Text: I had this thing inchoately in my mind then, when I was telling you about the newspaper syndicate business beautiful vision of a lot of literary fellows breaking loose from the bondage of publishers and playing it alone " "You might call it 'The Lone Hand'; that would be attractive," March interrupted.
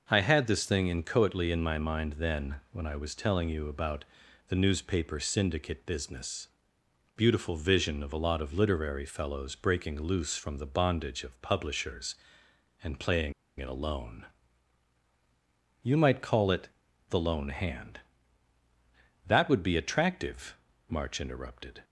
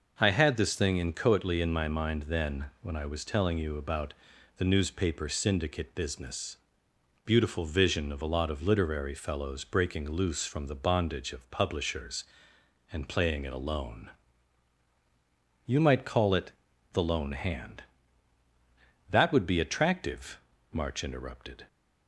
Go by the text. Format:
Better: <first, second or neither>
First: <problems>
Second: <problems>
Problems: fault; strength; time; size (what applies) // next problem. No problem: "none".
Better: second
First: pauses between "about" and "the"; noticeable; at 4.0 s; 0.46 s long // pauses between "business" and "beautiful"; noticeable; at 6.4 s; 0.68 s long // pauses between "playing" and "it"; slight; at 13.3 s; 0.27 s long // pauses between "it" and "The"; at 16.6 s; 0.42 s long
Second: pauses between "about" and "the"; noticeable; at 4.1 s; 0.46 s long // pauses between "business" and "beautiful"; noticeable; at 6.5 s; 0.68 s long // pauses between "it" and "The"; at 16.5 s; 0.42 s long